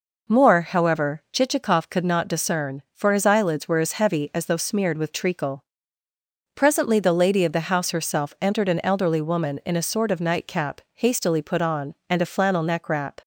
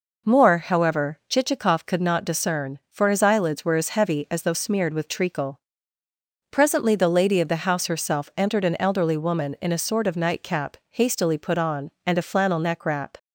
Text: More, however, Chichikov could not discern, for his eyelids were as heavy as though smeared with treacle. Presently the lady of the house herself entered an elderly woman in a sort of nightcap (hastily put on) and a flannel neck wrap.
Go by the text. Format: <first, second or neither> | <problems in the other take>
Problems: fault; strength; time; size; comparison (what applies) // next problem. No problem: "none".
neither | none